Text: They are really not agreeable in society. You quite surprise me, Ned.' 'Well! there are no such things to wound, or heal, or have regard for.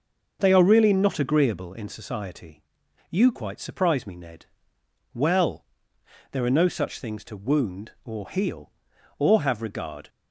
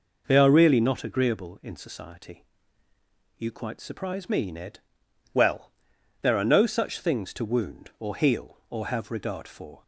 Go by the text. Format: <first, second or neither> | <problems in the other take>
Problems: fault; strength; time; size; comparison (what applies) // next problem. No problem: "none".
second | stops before "for"; at 10.0 s